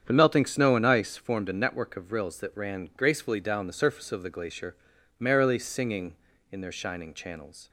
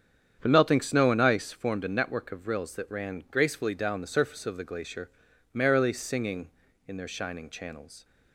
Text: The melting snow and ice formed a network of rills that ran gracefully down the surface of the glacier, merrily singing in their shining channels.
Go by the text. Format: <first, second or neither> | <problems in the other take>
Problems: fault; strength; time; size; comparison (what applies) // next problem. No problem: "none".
neither | starts louder than the rest; strong; the same in both